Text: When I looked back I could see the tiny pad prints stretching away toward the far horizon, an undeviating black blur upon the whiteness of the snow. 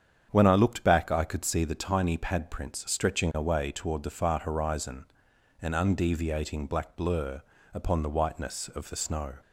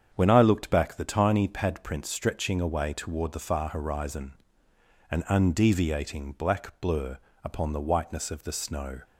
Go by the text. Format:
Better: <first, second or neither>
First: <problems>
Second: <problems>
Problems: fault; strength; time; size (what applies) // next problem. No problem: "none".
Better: first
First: starts louder than the rest; strong; until 1.3 s; 8 dB // pauses between "blur" and "upon"; slight; at 7.4 s; 0.32 s long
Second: starts louder than the rest; strong; until 1.1 s; 7.5 dB // skips "I could see"; at 0.9 s // pauses between "blur" and "upon"; slight; at 7.1 s; 0.28 s long